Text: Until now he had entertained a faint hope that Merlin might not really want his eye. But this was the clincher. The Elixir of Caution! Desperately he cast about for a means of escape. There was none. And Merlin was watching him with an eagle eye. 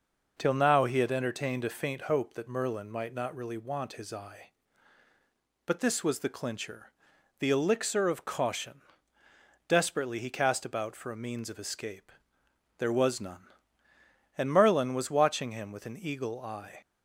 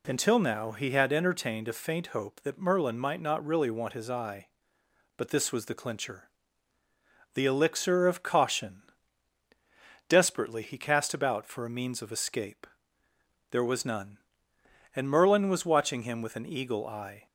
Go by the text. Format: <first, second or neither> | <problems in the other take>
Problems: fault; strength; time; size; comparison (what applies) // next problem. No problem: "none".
second | says "Till" for "Until"; at 0.3 s